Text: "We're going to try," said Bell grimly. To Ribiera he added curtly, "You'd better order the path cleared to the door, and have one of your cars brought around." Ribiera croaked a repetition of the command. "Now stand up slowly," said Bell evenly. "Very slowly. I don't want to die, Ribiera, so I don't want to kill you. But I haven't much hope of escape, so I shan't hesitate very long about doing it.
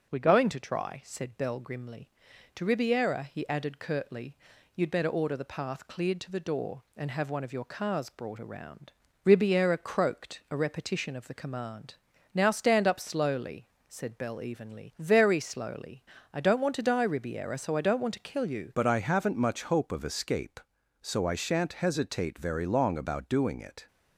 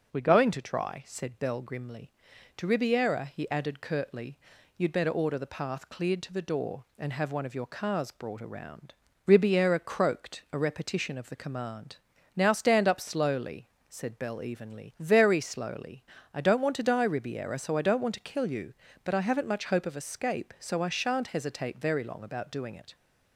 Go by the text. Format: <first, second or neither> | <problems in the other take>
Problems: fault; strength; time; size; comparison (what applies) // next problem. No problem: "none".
second | starts louder than the rest; noticeable; until 1.1 s; 6 dB; also in the second // changes voice at "But"; from 18.7 s on; 5.1 s long